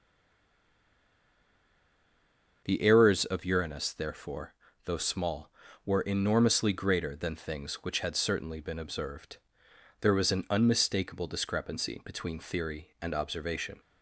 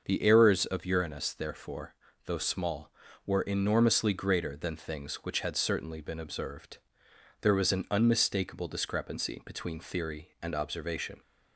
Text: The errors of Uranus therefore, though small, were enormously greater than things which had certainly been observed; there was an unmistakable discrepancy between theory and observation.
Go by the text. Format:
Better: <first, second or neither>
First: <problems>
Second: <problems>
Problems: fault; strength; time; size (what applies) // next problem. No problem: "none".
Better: second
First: stays silent before the first word; strong; until 2.6 s; 2.6 s long // starts louder than the rest; noticeable; until 3.6 s; 6 dB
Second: starts louder than the rest; noticeable; until 1.0 s; 6 dB